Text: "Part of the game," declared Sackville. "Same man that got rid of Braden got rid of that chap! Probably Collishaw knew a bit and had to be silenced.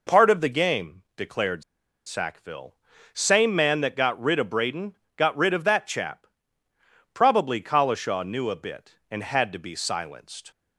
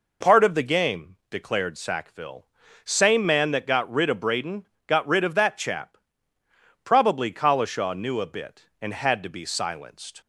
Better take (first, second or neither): second